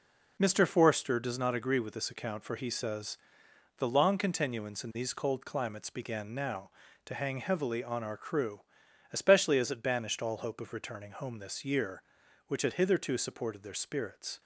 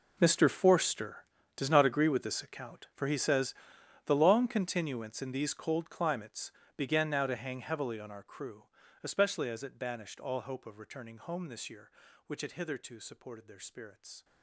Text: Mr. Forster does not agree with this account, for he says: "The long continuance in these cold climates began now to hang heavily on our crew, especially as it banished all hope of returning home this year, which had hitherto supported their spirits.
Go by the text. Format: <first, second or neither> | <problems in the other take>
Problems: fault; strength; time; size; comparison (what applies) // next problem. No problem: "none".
first | gets quieter; strong; throughout; 18 dB // pauses between "climates" and "began"; slight; at 6.5 s; 0.24 s long